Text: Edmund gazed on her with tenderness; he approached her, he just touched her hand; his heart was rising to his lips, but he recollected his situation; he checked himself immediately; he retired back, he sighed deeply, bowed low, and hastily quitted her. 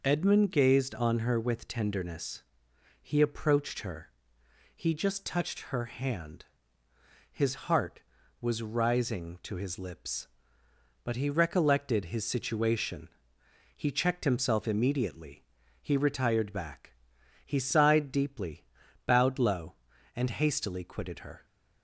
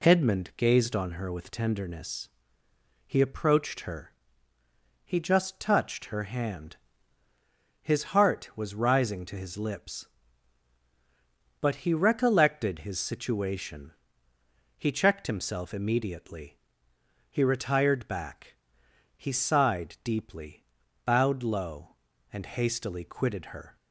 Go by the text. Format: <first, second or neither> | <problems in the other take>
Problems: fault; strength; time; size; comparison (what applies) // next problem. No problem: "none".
neither | none